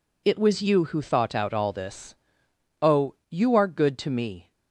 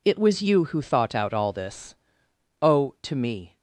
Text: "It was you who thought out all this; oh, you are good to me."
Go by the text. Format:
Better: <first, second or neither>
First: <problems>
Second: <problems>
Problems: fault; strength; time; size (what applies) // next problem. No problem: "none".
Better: first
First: none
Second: skips "you are good"; at 2.9 s